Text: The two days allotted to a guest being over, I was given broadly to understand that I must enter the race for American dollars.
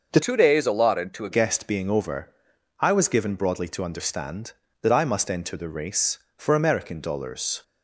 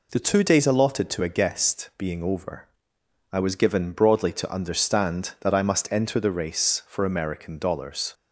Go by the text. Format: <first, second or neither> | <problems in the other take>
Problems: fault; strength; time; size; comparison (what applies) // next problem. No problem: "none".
second | changes voice from "two" to "a"; from 0.2 to 1.3 s; 1.1 s long